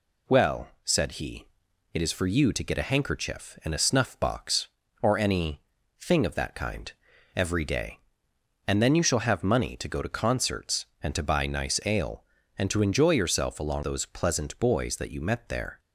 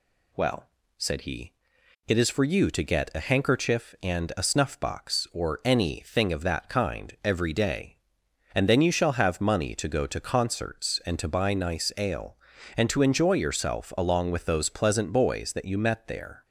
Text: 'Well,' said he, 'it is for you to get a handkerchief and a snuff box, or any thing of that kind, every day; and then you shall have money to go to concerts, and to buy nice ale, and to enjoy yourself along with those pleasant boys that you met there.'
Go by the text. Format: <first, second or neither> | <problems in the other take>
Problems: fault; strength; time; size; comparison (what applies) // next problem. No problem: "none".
second | pauses between "any" and "thing"; at 5.5 s; 0.40 s long // skips "with"; at 13.8 s